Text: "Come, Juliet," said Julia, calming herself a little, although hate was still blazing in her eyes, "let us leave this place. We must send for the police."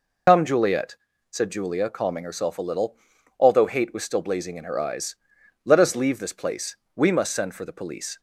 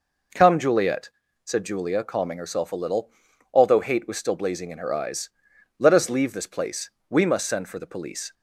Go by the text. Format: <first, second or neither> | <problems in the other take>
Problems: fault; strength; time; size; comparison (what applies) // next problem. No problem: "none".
second | loses the start of "Come"; at 0.2 s; 90 ms